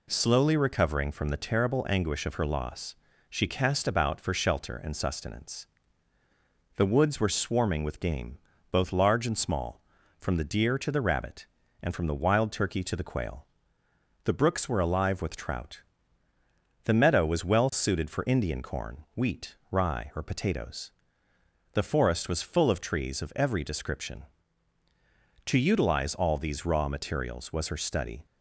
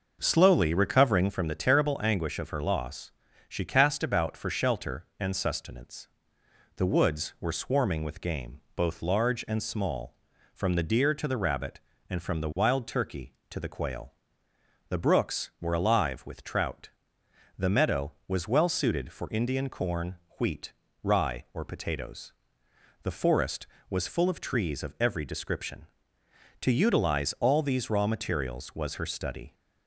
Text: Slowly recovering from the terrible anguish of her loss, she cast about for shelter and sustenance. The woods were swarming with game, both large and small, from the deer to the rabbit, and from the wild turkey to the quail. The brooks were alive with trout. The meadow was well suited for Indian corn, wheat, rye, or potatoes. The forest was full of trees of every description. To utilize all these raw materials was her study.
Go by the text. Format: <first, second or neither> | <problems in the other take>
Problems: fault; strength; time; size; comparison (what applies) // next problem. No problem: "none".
first | starts louder than the rest; noticeable; until 1.4 s; 6 dB